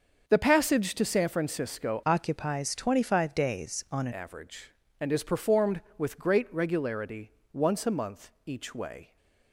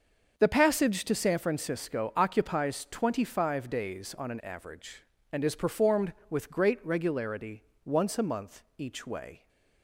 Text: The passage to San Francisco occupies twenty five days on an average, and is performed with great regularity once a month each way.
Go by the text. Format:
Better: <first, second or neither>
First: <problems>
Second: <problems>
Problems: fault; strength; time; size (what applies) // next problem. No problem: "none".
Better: second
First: starts louder than the rest; until 1.2 s; 6.5 dB // changes voice from "occupies" to "an"; from 2.0 to 4.1 s; 2.1 s long // pauses between "regularity" and "once"; slight; at 7.3 s; 0.20 s long // pauses between "month" and "each"; slight; at 8.2 s; 0.16 s long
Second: starts louder than the rest; until 1.3 s; 6.5 dB // pauses between "regularity" and "once"; slight; at 7.6 s; 0.20 s long // pauses between "month" and "each"; slight; at 8.6 s; 0.16 s long